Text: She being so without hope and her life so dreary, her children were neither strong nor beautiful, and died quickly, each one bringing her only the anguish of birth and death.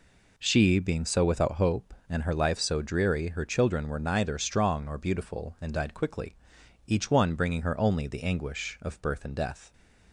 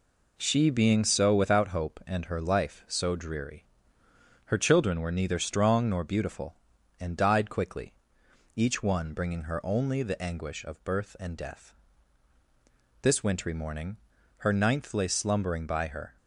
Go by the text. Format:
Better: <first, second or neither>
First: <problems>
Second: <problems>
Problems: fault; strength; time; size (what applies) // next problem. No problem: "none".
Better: first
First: none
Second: goes on to say "This wintry morning her ninth lay slumbering by her"; strong; from 13.0 s on; 3.1 s long